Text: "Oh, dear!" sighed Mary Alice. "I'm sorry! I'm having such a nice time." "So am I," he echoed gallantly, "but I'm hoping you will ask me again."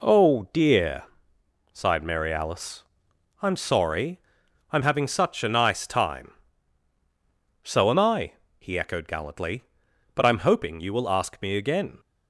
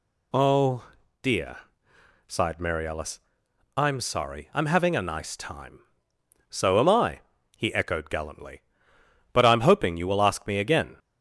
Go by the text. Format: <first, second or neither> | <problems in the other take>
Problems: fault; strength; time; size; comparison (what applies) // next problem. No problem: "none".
first | skips "such"; at 4.9 s